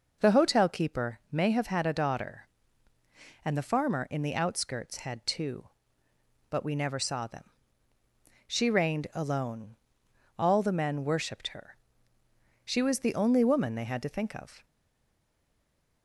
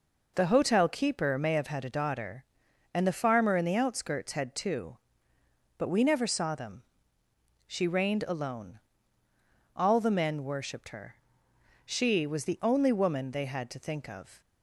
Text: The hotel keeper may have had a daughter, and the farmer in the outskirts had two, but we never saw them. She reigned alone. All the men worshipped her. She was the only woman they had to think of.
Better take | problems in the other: second | stays silent after the last word; noticeable; from 14.6 s on; 1.4 s long

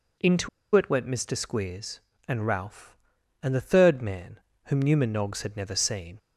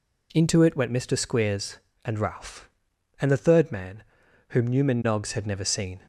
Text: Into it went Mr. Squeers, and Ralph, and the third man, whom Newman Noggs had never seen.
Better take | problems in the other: second | pauses between "Into" and "it"; slight; at 0.4 s; 0.26 s long

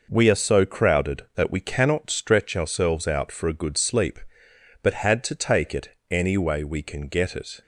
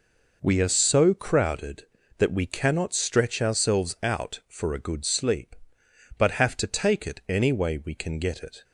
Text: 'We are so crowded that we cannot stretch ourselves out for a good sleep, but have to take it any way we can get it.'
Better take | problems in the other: second | says "had" for "have"; at 5.0 s // pauses between "it" and "any"; slight; at 5.8 s; 0.20 s long

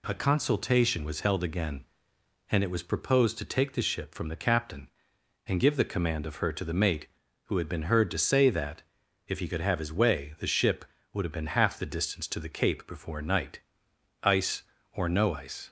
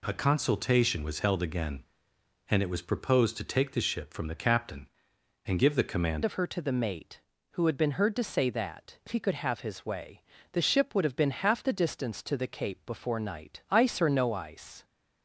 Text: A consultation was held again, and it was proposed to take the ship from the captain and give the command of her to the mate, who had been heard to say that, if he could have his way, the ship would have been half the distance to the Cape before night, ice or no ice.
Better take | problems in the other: first | changes voice at "of"; from 6.2 s on; 8.6 s long

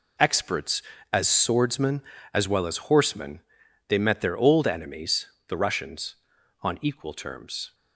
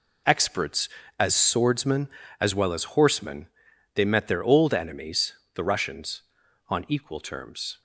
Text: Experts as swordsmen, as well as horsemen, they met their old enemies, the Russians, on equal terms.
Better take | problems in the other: neither | none

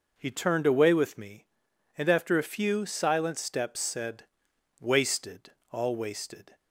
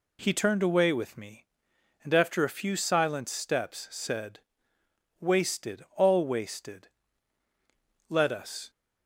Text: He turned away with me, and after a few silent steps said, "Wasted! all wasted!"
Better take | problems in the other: first | goes on to say "Let us"; from 8.0 s on; 0.60 s long

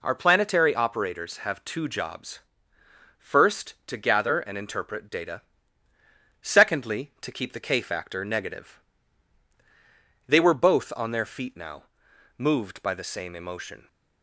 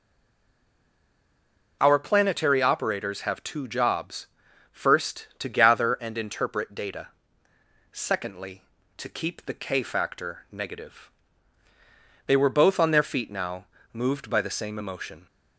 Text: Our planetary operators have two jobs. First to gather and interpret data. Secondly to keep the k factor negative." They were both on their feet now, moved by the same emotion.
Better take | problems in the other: first | stays silent before the first word; noticeable; until 1.8 s; 1.8 s long

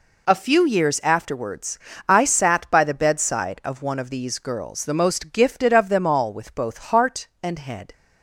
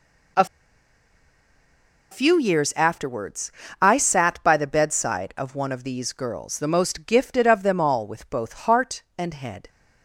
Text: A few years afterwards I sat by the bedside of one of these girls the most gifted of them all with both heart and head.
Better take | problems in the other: first | pauses between "A" and "few"; strong; at 0.4 s; 1.6 s long // pauses between "afterwards" and "I"; slight; at 3.5 s; 0.28 s long; slight in the first

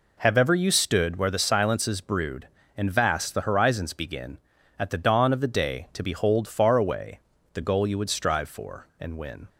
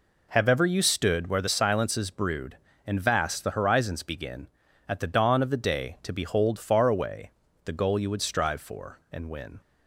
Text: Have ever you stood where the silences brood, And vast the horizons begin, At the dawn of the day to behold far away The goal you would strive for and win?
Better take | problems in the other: neither | pauses between "away" and "The"; slight; the same in both

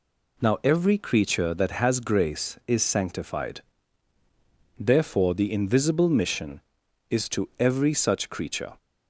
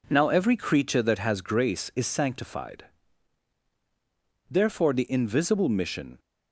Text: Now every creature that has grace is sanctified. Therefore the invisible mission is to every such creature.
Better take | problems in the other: first | stops before "is to every such creature"; at 6.1 s

